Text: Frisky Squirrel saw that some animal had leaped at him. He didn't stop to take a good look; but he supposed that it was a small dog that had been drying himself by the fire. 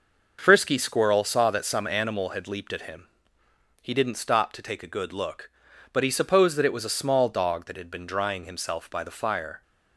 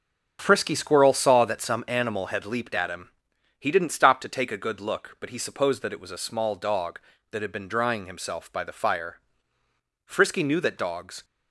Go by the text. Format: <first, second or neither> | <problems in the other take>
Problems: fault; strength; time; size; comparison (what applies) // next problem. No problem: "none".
first | starts louder than the rest; until 1.4 s; 7 dB // goes on to say "Frisky knew that dogs"; noticeable; from 10.0 s on; 1.1 s long